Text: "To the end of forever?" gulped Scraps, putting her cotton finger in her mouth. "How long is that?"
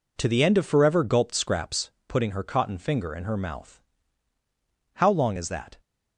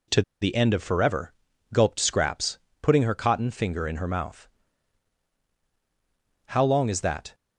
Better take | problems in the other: first | pauses between "To" and "the"; slight; at 0.2 s; 0.18 s long

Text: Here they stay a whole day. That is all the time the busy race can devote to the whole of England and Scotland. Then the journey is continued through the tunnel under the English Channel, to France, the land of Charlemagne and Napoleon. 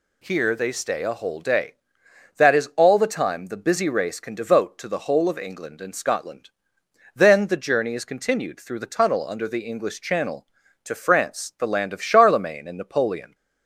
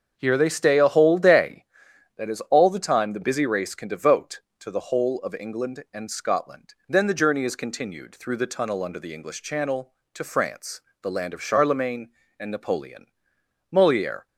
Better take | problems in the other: first | starts louder than the rest; until 1.1 s; 6.5 dB // goes on to say "Moliere"; from 13.7 s on; 0.56 s long

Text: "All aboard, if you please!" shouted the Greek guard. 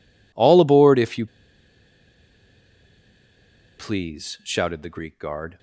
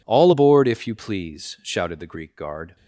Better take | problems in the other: second | pauses between "you" and "please"; strong; at 1.2 s; 2.5 s long

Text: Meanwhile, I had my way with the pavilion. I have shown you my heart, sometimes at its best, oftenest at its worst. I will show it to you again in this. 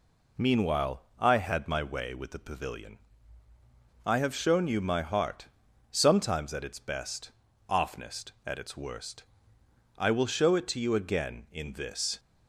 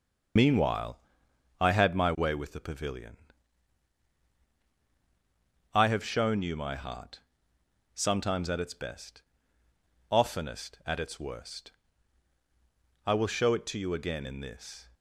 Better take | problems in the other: first | loses the start of "Meanwhile"; at 0.3 s; 60 ms // starts louder than the rest; until 1.9 s; 6 dB

